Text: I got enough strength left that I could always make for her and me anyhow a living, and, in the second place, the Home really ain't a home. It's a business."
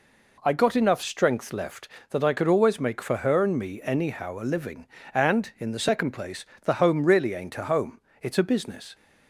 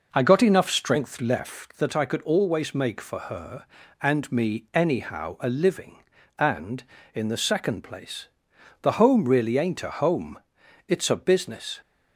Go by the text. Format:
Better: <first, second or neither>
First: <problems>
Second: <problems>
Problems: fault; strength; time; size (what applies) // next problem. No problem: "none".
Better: first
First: none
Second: starts louder than the rest; noticeable; until 1.5 s; 5.5 dB